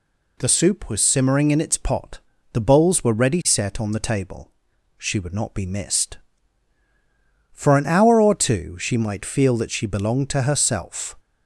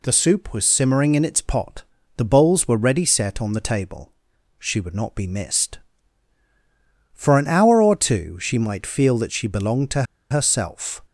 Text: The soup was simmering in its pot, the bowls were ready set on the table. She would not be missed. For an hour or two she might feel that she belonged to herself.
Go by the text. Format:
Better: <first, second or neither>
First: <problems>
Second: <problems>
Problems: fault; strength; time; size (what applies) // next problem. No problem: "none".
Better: first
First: none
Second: pauses between "to" and "herself"; slight; at 10.0 s; 0.27 s long